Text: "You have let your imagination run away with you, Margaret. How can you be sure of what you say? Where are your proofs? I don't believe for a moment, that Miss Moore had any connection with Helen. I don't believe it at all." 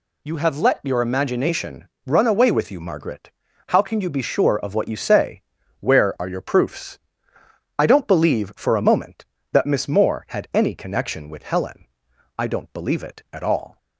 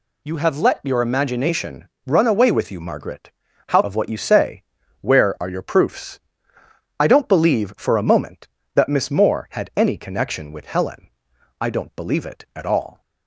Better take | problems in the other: first | pauses between "imagination" and "run"; slight; at 1.8 s; 0.18 s long; slight in the first // skips "can you be sure"; at 3.8 s

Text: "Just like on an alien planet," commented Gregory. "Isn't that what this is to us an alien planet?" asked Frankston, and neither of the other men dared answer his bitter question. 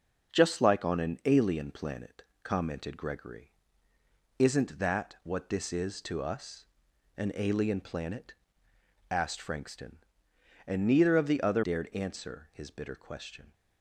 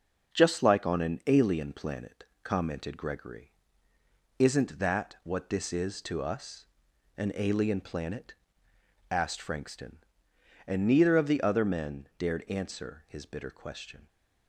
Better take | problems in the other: second | starts louder than the rest; until 1.3 s; 6 dB; also in the second // pauses between "us" and "an"; noticeable; at 6.6 s; 0.50 s long; noticeable in the second // skips "men"; at 11.6 s

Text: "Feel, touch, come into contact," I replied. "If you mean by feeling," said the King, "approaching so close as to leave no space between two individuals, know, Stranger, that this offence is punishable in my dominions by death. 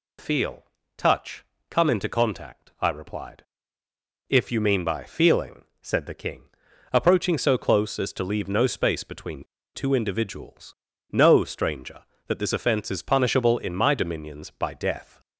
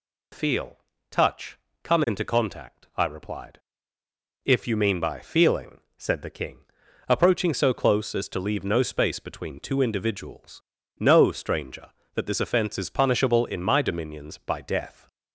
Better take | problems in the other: second | pauses between "between" and "two"; slight; at 9.4 s; 0.28 s long

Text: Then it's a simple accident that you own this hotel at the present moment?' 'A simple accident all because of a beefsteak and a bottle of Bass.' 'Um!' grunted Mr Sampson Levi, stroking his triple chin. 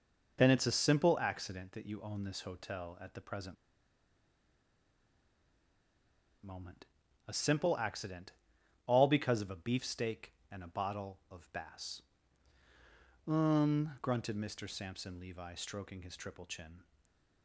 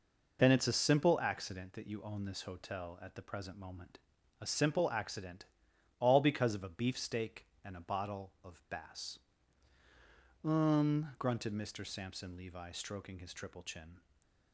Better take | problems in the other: second | pauses between "present" and "moment"; strong; at 3.5 s; 2.8 s long // pauses between "accident" and "all"; noticeable; at 8.3 s; 0.54 s long; noticeable in the second // stays silent after the last word; slight; from 16.8 s on; 0.6 s long; slight in the second

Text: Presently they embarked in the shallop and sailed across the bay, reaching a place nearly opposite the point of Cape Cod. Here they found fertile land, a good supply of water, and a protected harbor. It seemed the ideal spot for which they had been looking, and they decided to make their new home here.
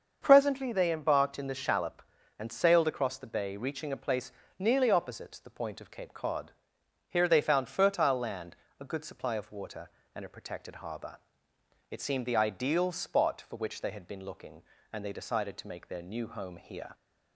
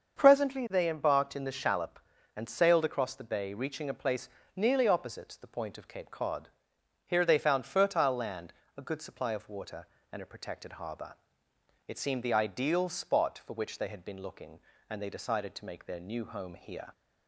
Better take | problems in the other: neither | starts louder than the rest; the same in both // pauses between "place" and "nearly"; slight; the same in both

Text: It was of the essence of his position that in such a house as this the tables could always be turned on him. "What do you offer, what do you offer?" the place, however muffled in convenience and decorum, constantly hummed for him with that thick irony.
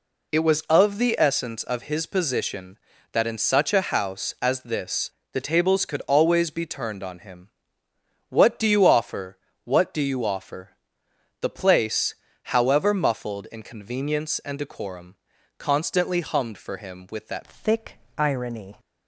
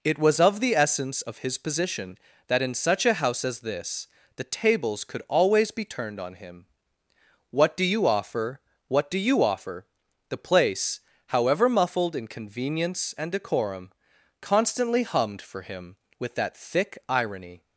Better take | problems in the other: second | pauses between "this" and "the"; slight; at 5.1 s; 0.22 s long; slight in the second // changes voice at "thick"; from 17.4 s on; 1.3 s long // pauses between "thick" and "irony"; slight; at 17.9 s; 0.18 s long

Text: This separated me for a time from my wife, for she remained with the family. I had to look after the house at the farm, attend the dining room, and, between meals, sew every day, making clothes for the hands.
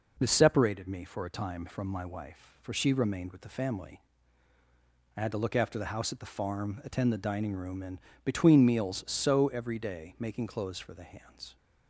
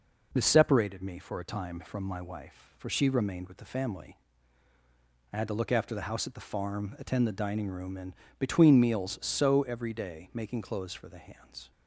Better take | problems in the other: neither | none

